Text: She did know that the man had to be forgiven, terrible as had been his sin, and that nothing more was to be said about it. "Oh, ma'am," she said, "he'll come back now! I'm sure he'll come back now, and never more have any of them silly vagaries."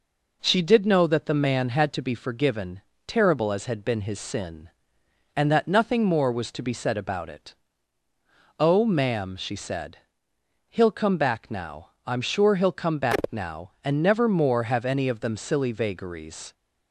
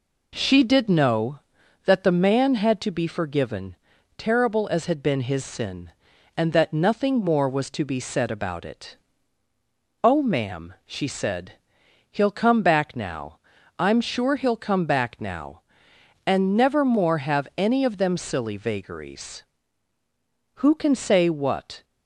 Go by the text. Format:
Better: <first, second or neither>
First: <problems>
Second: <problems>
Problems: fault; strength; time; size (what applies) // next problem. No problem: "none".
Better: first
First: none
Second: goes on to say "Who can say what"; noticeable; from 20.5 s on; 1.2 s long